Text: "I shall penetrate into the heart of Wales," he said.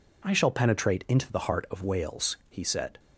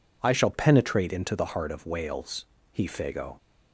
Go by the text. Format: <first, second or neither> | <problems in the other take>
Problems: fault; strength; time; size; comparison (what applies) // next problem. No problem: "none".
first | says "fago" for "said"; at 2.8 s